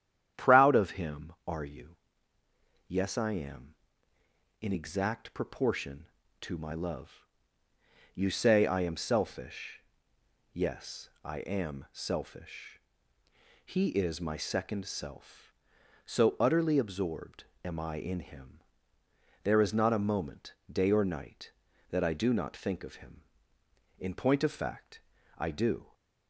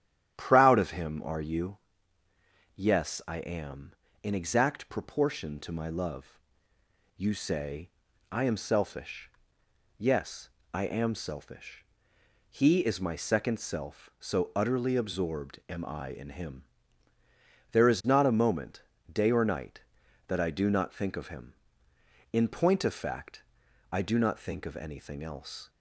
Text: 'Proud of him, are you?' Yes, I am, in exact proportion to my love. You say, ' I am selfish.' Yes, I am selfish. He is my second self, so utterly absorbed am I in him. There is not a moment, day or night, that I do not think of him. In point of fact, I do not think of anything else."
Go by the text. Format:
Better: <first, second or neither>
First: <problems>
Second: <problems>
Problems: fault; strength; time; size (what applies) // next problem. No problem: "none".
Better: second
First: starts louder than the rest; strong; until 1.5 s; 10 dB // pauses between "absorbed" and "am"; slight; at 17.4 s; 0.20 s long // stops before "not think of anything else"; at 25.9 s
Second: starts louder than the rest; strong; until 1.3 s; 11 dB